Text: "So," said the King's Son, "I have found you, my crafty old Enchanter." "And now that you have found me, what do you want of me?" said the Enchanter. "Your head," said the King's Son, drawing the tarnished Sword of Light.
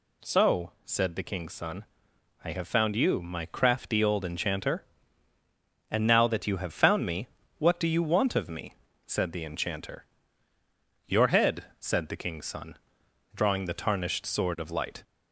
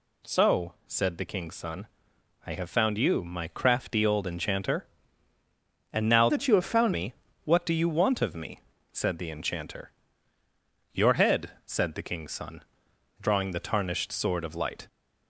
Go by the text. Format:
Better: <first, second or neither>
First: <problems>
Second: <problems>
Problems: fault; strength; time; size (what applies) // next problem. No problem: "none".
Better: first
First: none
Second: changes voice from "that" to "found"; from 6.2 to 6.9 s; 0.7 s long